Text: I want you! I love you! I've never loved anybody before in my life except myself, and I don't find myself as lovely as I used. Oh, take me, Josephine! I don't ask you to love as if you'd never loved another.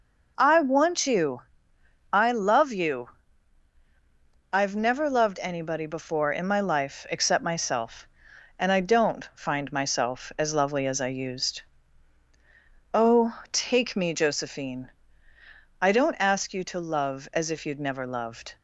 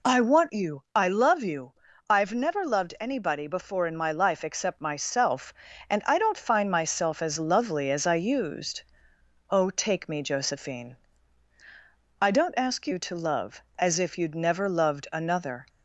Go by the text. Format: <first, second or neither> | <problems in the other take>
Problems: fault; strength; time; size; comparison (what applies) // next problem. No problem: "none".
second | stops before "another"; at 18.5 s